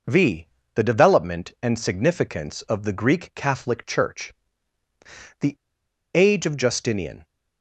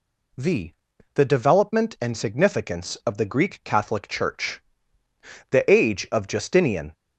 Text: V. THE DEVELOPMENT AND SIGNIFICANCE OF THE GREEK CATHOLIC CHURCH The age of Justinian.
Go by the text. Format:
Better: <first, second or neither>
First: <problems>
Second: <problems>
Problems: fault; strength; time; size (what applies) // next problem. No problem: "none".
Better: second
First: pauses between "CHURCH" and "The"; at 4.3 s; 1.0 s long // pauses between "The" and "age"; noticeable; at 5.5 s; 0.60 s long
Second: pauses between "CHURCH" and "The"; noticeable; at 4.6 s; 0.88 s long